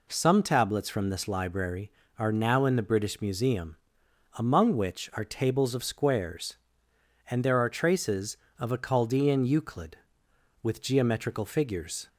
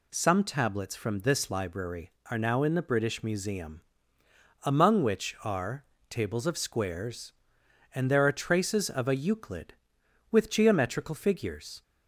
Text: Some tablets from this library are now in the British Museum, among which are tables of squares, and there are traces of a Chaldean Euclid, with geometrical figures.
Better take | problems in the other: first | pauses between "are" and "tables"; slight; at 5.8 s; 0.26 s long // skips "Chaldean"; at 9.1 s

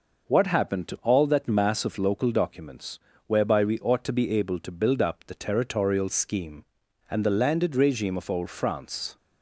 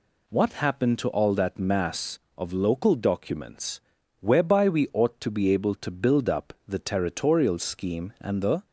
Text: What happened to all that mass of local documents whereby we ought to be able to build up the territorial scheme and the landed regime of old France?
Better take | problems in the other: first | pauses between "documents" and "whereby"; at 3.8 s; 0.38 s long; slight in the first // stops before "landed regime of old France"; at 8.6 s

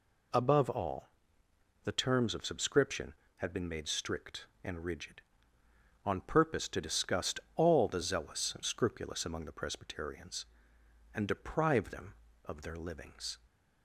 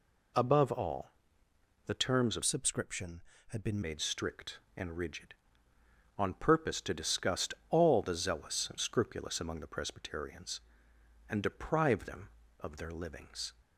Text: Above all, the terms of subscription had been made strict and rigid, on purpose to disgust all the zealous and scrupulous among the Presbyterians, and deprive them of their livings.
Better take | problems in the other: first | changes voice from "subscription" to "been"; from 2.4 to 3.8 s; 1.4 s long // pauses between "disgust" and "all"; slight; at 7.5 s; 0.16 s long; slight in the first

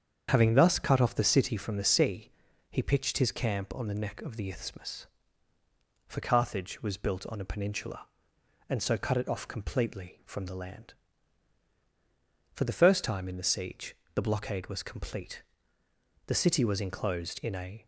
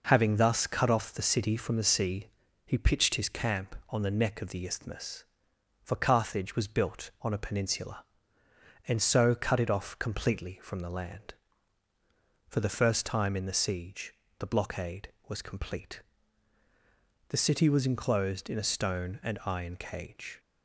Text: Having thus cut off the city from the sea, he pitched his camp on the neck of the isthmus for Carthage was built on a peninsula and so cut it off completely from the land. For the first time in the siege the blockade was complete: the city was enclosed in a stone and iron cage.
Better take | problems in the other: second | starts louder than the rest; strong; until 1.3 s; 7.5 dB // pauses between "siege" and "the"; slight; at 13.9 s; 0.18 s long; slight in the second // stops before "stone and iron cage"; at 17.8 s

